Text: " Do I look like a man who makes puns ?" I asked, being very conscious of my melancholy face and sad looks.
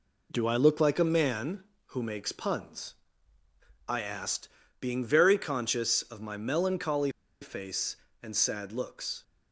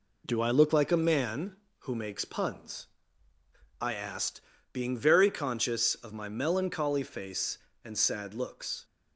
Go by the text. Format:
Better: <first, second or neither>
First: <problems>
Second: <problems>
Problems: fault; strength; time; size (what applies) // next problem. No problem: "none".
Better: second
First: pauses between "melancholy" and "face"; slight; at 7.1 s; 0.30 s long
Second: none